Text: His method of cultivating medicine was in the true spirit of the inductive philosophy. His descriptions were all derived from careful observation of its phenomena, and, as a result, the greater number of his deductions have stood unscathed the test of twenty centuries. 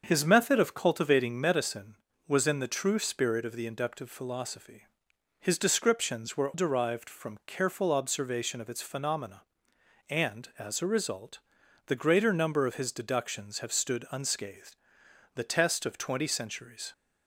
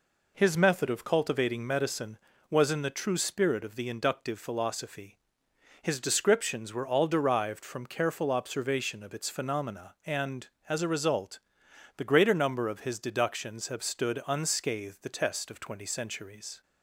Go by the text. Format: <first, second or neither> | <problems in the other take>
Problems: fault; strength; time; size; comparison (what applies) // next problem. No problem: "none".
second | starts louder than the rest; until 1.0 s; 6.5 dB // skips "all"; at 6.5 s // pauses between "unscathed" and "the"; noticeable; at 14.7 s; 0.60 s long